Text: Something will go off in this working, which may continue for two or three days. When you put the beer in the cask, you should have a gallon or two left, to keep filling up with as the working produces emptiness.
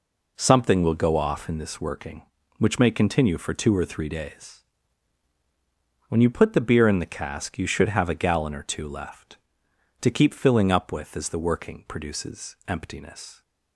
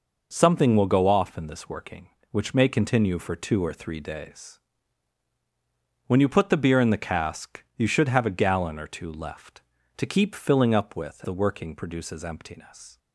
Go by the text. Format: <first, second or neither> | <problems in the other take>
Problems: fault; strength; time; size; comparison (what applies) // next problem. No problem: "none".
first | skips "as"; at 11.2 s